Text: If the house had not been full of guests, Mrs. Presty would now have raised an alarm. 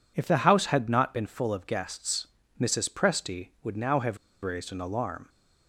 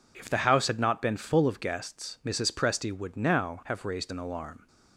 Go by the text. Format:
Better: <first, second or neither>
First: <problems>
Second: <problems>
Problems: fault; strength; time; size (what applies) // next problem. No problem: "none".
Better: second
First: pauses between "have" and "raised"; slight; at 4.1 s; 0.25 s long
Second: none